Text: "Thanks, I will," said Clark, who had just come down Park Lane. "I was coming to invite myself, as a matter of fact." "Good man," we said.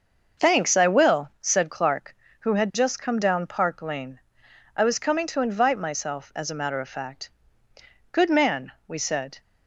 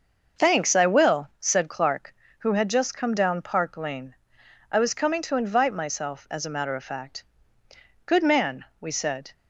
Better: neither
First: starts louder than the rest; until 1.5 s; 6 dB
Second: starts louder than the rest; until 1.5 s; 6 dB

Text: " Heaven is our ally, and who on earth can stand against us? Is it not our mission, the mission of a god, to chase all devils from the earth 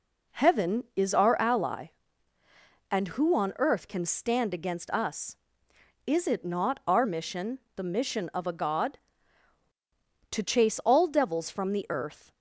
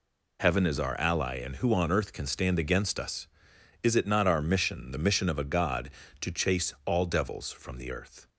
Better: first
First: none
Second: changes voice at "Heaven"; from 0.3 s on; 7.9 s long

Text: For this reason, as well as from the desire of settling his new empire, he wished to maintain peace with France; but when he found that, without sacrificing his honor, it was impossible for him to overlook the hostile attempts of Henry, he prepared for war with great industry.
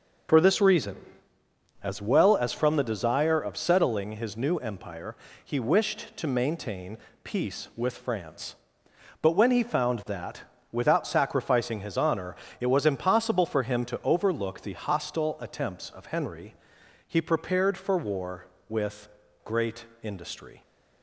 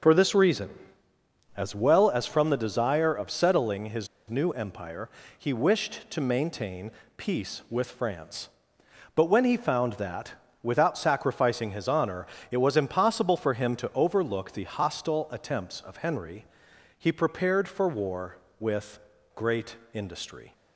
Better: first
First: starts louder than the rest; noticeable; until 2.1 s; 6 dB // pauses between "maintain" and "peace"; slight; at 6.9 s; 0.26 s long // pauses between "with" and "great"; slight; at 19.0 s; 0.36 s long // pauses between "great" and "industry"; slight; at 19.8 s; 0.16 s long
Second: starts louder than the rest; noticeable; until 1.9 s; 6 dB // pauses between "his" and "new"; slight; at 4.0 s; 0.22 s long // pauses between "maintain" and "peace"; slight; at 6.9 s; 0.26 s long // pauses between "with" and "great"; slight; at 18.9 s; 0.36 s long // pauses between "great" and "industry"; slight; at 19.7 s; 0.16 s long

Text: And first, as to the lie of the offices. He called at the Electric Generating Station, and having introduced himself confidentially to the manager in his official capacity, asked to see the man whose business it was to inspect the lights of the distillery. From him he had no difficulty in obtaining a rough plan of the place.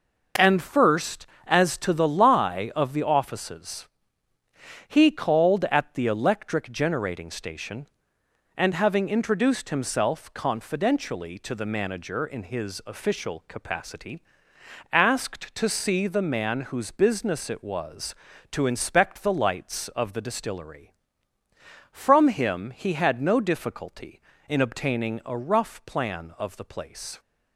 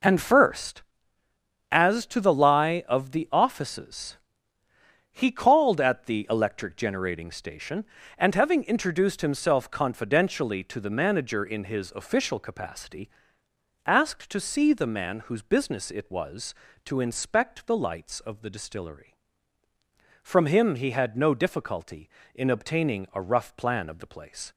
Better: neither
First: none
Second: none

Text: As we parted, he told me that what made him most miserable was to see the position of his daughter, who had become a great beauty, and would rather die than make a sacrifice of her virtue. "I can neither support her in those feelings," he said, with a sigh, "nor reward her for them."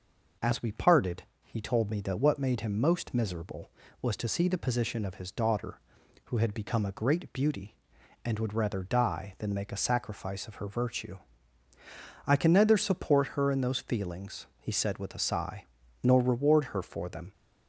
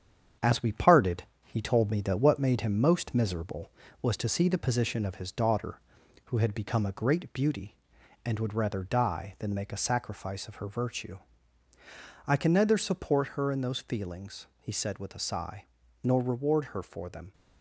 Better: first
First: none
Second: gets quieter; noticeable; throughout; 4.5 dB

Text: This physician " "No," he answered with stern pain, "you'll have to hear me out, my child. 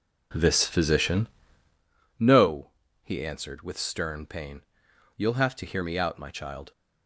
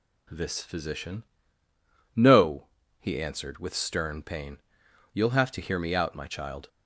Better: second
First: starts louder than the rest; noticeable; until 1.9 s; 5 dB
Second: none

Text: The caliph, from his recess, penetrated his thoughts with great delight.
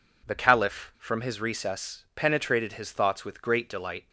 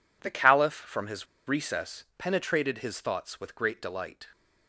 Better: first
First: none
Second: pauses between "his" and "recess"; slight; at 1.2 s; 0.21 s long

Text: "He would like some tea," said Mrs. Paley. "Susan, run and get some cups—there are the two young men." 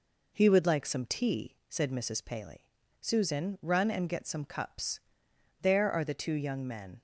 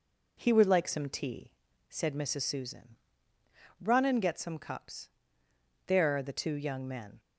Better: first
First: none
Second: skips "Paley"; at 2.4 s

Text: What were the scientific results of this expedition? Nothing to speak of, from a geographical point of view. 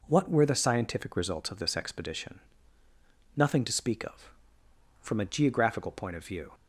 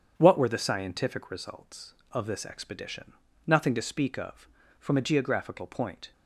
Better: first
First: none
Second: starts louder than the rest; strong; until 1.1 s; 8 dB // stops before "of view"; at 6.1 s

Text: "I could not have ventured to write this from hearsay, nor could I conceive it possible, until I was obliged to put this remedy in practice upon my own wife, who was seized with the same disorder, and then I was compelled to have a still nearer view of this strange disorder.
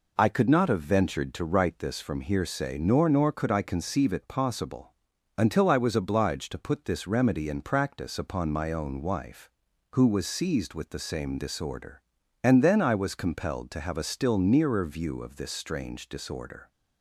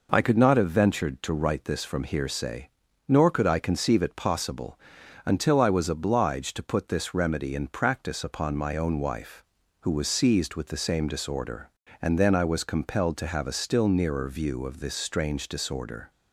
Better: second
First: says "nor" twice; at 3.0 s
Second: none

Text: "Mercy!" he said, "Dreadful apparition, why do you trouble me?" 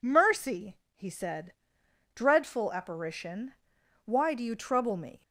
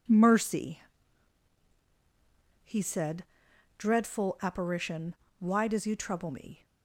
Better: first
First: none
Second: says "does" for "do"; at 5.6 s

